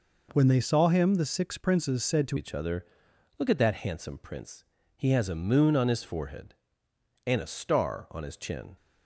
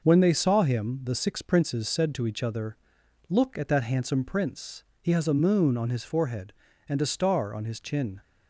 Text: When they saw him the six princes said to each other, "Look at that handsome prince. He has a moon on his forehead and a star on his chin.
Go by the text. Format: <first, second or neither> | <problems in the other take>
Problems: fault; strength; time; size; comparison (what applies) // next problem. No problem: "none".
second | changes voice at "each"; from 2.3 s on; 6.4 s long